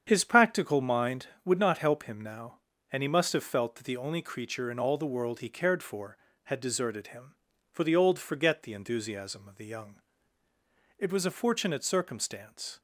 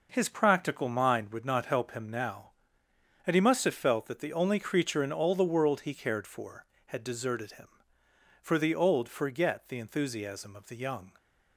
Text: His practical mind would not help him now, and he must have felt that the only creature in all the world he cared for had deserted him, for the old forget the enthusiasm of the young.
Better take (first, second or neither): second